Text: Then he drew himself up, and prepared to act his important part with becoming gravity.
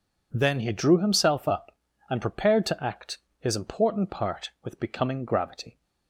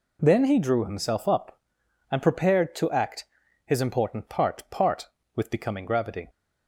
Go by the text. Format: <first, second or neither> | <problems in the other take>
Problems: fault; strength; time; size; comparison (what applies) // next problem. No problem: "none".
first | pauses between "act" and "his"; at 3.2 s; 0.40 s long; slight in the first // says "part" twice; at 4.6 s